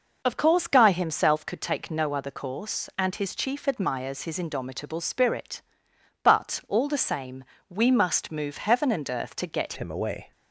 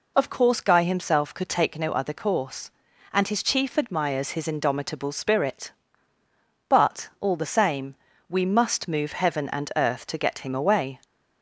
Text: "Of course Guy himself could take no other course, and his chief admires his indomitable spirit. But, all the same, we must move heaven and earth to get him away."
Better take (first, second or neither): second